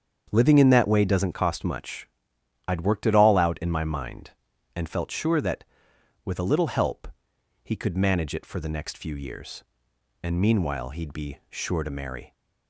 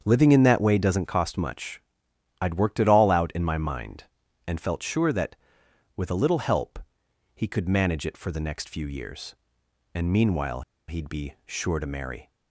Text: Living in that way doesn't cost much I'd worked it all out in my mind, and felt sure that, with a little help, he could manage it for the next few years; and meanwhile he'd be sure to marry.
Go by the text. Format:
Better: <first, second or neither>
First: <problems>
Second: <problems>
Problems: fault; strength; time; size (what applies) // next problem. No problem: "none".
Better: first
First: starts louder than the rest; strong; until 1.3 s; 7.5 dB // pauses between "much" and "I'd"; noticeable; at 2.0 s; 0.60 s long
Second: starts louder than the rest; strong; until 1.0 s; 7.5 dB // pauses between "much" and "I'd"; noticeable; at 1.7 s; 0.60 s long // pauses between "meanwhile" and "he'd"; slight; at 10.6 s; 0.26 s long